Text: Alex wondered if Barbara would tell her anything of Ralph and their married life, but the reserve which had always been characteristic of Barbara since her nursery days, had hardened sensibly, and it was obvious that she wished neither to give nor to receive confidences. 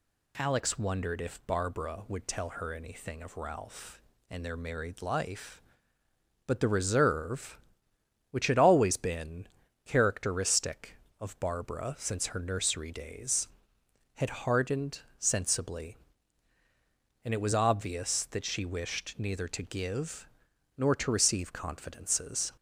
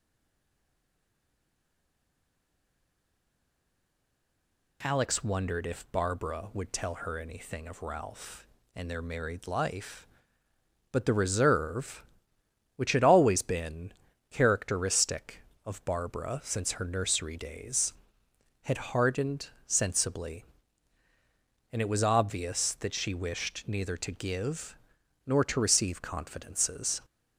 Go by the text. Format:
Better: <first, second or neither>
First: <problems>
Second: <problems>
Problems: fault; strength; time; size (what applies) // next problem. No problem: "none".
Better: first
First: pauses between "been" and "characteristic"; at 9.4 s; 0.40 s long // pauses between "hardened" and "sensibly"; slight; at 14.9 s; 0.18 s long // pauses between "give" and "nor"; noticeable; at 20.2 s; 0.50 s long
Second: stays silent before the first word; strong; until 4.8 s; 4.8 s long // pauses between "been" and "characteristic"; at 13.9 s; 0.40 s long // pauses between "hardened" and "sensibly"; slight; at 19.4 s; 0.18 s long // pauses between "give" and "nor"; noticeable; at 24.7 s; 0.50 s long